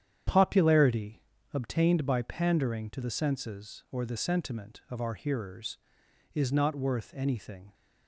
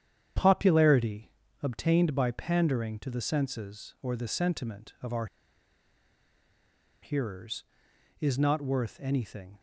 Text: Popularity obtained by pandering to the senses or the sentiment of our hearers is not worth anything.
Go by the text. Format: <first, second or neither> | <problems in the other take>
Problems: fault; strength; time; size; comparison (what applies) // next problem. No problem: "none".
first | starts louder than the rest; strong; until 1.7 s; 9.5 dB; strong in the first // pauses between "Popularity" and "obtained"; slight; at 1.3 s; 0.32 s long; slight in the first // pauses between "our" and "hearers"; strong; at 5.2 s; 1.7 s long